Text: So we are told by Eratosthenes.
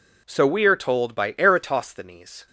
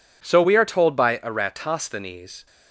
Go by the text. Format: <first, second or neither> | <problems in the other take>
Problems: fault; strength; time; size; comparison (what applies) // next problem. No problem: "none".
neither | none